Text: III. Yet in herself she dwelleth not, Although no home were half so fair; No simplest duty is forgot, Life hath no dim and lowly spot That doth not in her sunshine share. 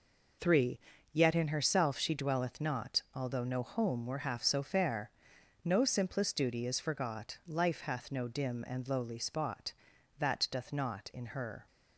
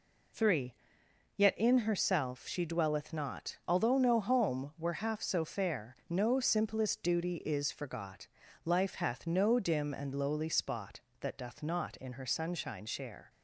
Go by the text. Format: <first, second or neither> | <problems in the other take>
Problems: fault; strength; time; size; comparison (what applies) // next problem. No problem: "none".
second | stops before "sunshine share"; at 11.6 s